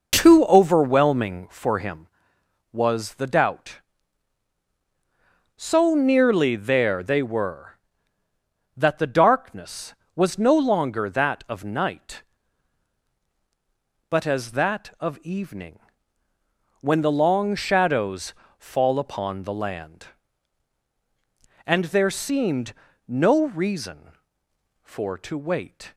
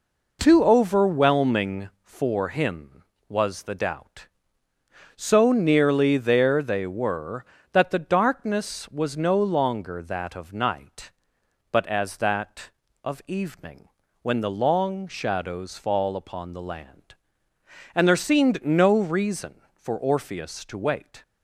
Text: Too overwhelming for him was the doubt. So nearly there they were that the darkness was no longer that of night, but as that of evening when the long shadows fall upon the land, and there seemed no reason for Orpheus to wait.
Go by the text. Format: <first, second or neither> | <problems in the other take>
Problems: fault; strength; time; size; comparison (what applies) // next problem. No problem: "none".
second | pauses between "evening" and "when"; at 15.7 s; 1.0 s long; slight in the second // pauses between "shadows" and "fall"; slight; at 18.3 s; 0.22 s long // pauses between "seemed" and "no"; slight; at 22.7 s; 0.36 s long // skips "Orpheus"; at 25.1 s